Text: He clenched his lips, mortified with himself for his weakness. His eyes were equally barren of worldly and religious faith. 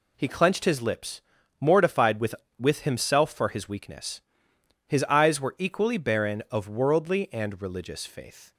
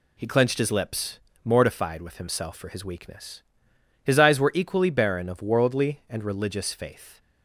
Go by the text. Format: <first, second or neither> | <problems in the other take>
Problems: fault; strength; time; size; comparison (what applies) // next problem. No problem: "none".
second | says "with" twice; at 2.5 s